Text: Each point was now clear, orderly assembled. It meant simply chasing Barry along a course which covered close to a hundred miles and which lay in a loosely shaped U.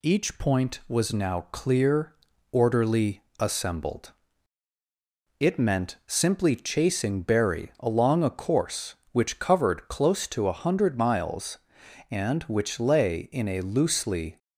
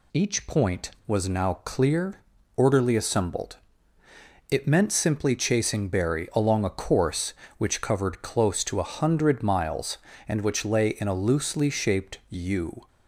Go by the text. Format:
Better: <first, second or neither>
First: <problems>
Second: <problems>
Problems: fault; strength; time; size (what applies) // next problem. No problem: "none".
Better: second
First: pauses between "orderly" and "assembled"; slight; at 3.2 s; 0.16 s long // stops before "shaped U"; at 14.3 s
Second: none